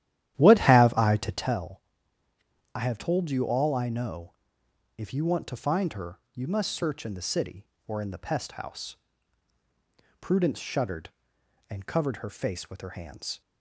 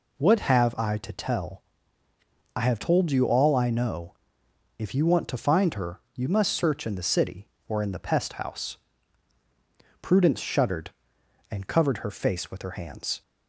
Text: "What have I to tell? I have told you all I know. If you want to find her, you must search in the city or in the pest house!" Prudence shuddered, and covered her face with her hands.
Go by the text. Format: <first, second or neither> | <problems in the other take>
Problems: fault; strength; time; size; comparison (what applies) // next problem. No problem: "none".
second | starts louder than the rest; strong; until 1.7 s; 12 dB